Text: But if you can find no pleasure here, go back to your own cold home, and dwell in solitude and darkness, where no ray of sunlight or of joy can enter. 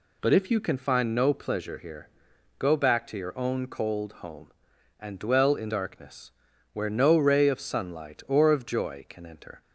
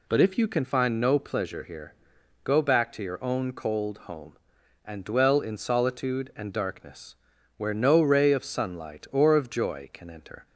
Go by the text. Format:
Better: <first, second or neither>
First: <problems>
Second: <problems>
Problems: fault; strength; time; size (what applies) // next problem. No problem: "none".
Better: second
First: skips "solitude and"; at 5.7 s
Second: none